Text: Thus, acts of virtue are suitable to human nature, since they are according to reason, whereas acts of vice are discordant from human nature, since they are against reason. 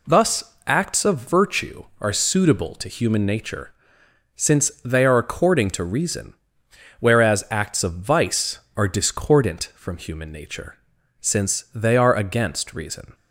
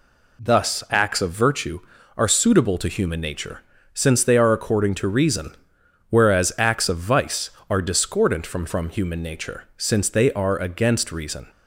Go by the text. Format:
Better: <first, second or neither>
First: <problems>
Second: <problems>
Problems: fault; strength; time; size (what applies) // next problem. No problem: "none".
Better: first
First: none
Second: says "from" twice; at 8.6 s